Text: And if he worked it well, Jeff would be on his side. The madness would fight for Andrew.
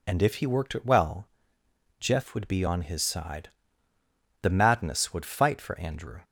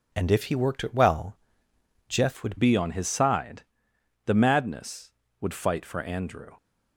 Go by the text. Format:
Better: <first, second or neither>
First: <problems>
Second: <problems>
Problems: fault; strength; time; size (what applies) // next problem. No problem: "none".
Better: first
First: none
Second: changes voice at "be"; from 2.5 s on; 4.0 s long